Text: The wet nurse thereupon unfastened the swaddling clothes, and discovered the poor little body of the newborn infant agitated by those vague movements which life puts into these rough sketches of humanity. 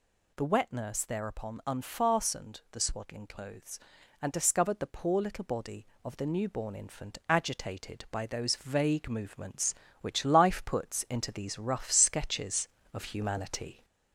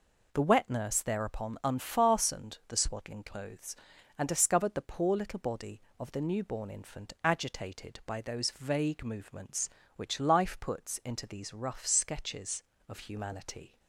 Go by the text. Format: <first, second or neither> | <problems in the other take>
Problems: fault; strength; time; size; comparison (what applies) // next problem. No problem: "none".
second | gets louder; slight; throughout; 2 dB